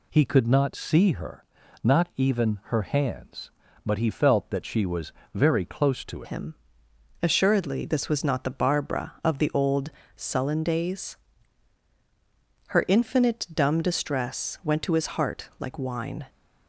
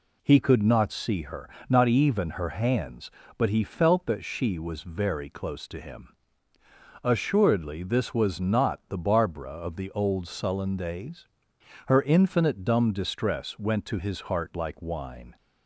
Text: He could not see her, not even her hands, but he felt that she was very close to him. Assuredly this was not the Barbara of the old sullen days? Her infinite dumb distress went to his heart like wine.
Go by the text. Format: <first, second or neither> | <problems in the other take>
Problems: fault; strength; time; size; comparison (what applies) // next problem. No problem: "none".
second | pauses between "was" and "very"; slight; at 5.1 s; 0.20 s long // changes voice at "him"; from 6.2 s on; 10.0 s long // pauses between "old" and "sullen"; slight; at 9.8 s; 0.28 s long